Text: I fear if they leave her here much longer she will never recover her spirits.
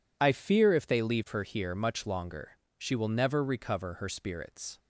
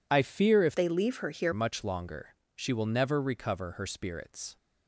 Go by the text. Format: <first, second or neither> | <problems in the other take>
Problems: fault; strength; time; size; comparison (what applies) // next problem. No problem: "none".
first | changes voice from "they" to "here"; from 0.7 to 1.5 s; 0.8 s long // pauses between "longer" and "she"; slight; at 2.3 s; 0.20 s long; slight in the first